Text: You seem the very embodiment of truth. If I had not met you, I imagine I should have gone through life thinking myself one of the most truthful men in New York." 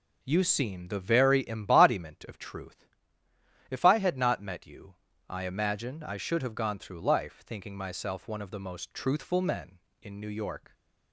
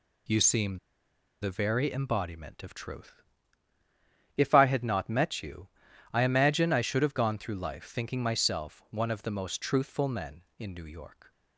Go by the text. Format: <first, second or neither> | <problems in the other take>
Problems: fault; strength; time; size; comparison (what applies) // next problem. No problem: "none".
first | pauses between "seem" and "the"; noticeable; at 0.7 s; 0.63 s long